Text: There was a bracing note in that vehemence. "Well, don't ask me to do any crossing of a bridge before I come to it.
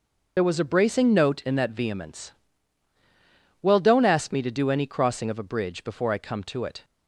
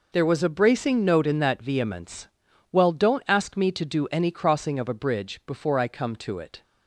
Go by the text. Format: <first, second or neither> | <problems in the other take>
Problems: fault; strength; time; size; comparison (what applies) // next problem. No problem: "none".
second | loses the start of "There"; at 0.3 s; 45 ms